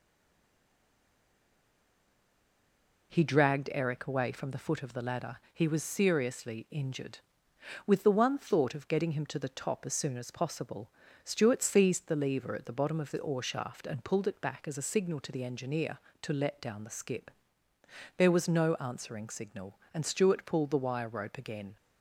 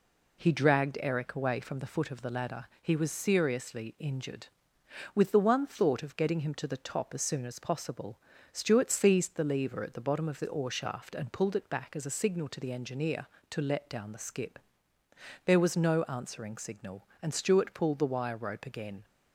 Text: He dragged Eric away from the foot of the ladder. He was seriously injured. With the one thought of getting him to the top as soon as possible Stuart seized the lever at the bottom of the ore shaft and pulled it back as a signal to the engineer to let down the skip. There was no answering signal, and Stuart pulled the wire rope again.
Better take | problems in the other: second | stays silent before the first word; strong; until 3.1 s; 3.1 s long // pauses between "possible" and "Stuart"; slight; at 10.8 s; 0.36 s long; slight in the second

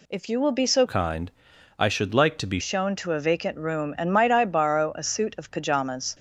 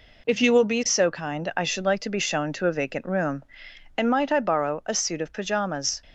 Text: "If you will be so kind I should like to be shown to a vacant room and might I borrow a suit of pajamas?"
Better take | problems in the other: second | changes voice from "kind" to "be"; from 0.8 to 2.5 s; 1.7 s long // pauses between "kind" and "I"; noticeable; at 1.2 s; 0.48 s long

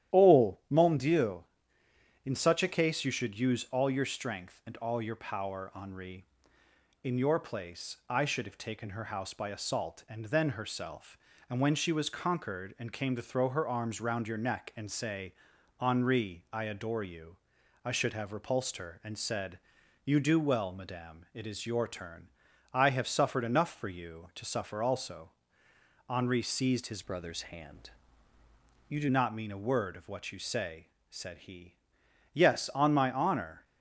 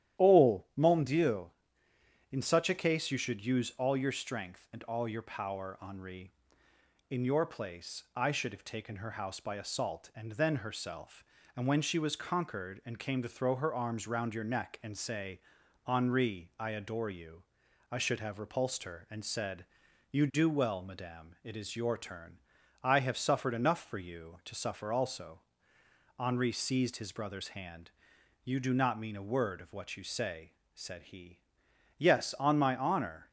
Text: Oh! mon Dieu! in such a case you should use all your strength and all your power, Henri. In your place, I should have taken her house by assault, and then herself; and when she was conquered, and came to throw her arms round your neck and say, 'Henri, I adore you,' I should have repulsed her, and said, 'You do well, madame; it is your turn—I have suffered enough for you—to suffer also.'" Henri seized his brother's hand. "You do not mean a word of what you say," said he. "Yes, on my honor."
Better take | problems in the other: second | starts louder than the rest; strong; until 1.2 s; 11.5 dB; strong in the second // changes voice from "brother's" to "do"; from 27.0 to 29.0 s; 2.0 s long

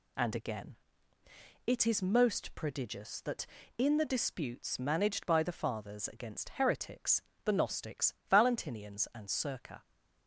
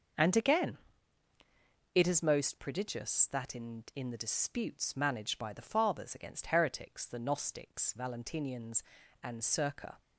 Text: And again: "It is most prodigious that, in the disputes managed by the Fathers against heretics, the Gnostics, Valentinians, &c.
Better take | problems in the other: first | starts louder than the rest; until 2.3 s; 6.5 dB // says "in" twice; at 3.9 s

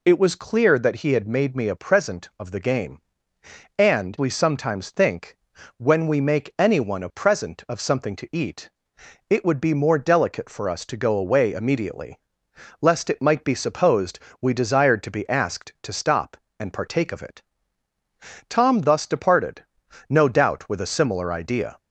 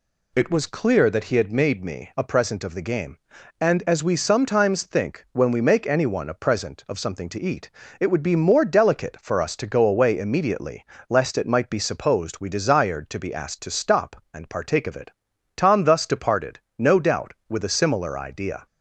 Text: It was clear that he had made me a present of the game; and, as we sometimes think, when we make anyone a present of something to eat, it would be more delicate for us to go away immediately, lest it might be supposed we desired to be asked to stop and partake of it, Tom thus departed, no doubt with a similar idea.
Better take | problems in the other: second | skips "as"; at 4.1 s // pauses between "supposed" and "we"; slight; at 14.1 s; 0.24 s long

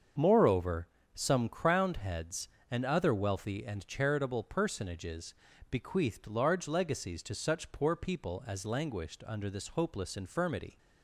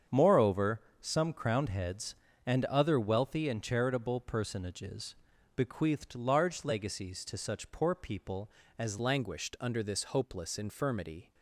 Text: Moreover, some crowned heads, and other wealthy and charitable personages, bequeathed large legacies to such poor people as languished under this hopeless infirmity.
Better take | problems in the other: first | starts louder than the rest; strong; until 1.3 s; 7.5 dB; also in the first // changes voice at "languished"; from 8.9 s on; 2.4 s long

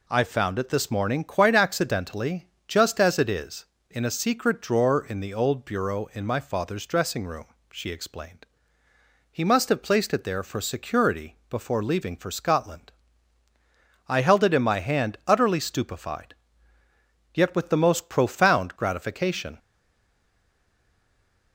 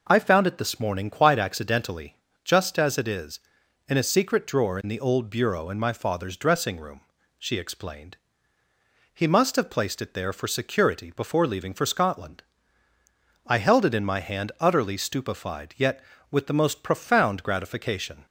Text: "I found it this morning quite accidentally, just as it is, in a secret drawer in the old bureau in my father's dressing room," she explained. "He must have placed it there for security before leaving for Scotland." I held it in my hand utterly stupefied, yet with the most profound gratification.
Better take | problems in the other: second | stays silent after the last word; noticeable; from 19.5 s on; 2.0 s long

